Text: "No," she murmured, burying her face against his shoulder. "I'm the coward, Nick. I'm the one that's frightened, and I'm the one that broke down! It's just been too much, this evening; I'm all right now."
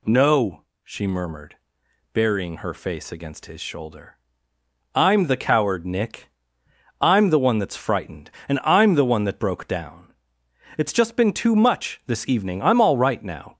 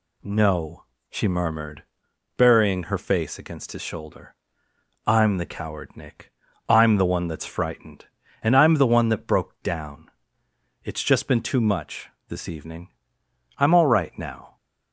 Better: neither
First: none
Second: none

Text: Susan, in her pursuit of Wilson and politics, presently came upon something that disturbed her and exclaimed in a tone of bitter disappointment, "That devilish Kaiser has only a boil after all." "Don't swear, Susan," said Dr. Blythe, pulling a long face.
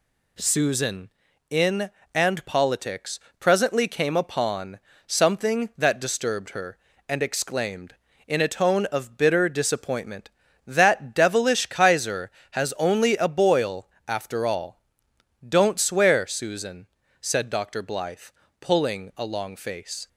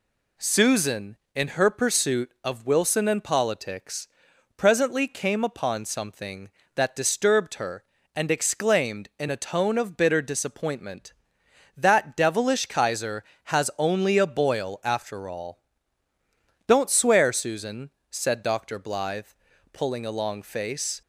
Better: second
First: skips "her pursuit of Wilson"; at 2.0 s // pauses between "upon" and "something"; slight; at 4.7 s; 0.28 s long // pauses between "boil" and "after"; slight; at 13.8 s; 0.20 s long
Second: none

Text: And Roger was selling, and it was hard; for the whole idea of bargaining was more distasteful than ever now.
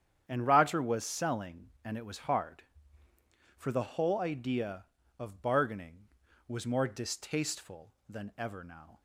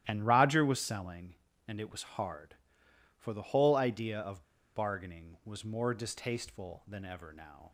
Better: first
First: starts louder than the rest; strong; until 1.3 s; 9 dB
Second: starts louder than the rest; strong; until 1.0 s; 12.5 dB // pauses between "of" and "bargaining"; slight; at 4.4 s; 0.32 s long

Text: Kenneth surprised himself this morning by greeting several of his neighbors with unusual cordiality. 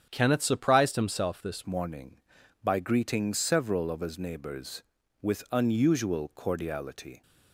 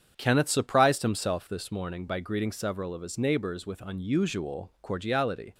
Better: second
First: starts louder than the rest; strong; until 1.1 s; 8.5 dB // changes voice at "morning"; from 1.6 s on; 5.6 s long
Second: starts louder than the rest; strong; until 1.1 s; 8 dB

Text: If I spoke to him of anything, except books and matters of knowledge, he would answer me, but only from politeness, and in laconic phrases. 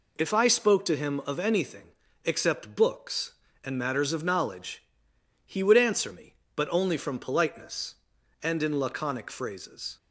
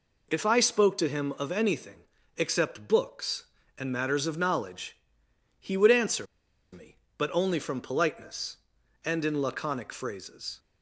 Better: first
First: none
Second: pauses between "answer" and "me"; noticeable; at 6.2 s; 0.46 s long

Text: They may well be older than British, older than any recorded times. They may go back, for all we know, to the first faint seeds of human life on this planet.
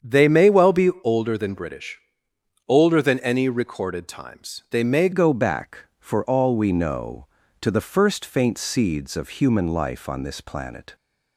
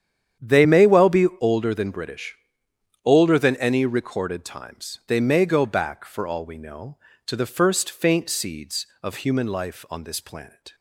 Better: second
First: starts louder than the rest; strong; until 1.1 s; 7.5 dB // changes voice at "go"; from 5.1 s on; 5.8 s long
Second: starts louder than the rest; strong; until 1.5 s; 9 dB

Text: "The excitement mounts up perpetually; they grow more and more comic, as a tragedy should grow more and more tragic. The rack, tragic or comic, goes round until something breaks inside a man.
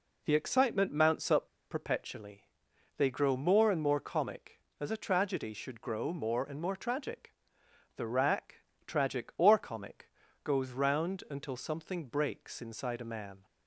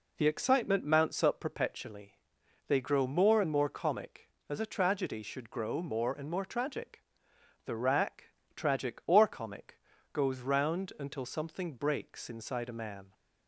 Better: second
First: pauses between "up" and "perpetually"; slight; at 1.4 s; 0.22 s long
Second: none

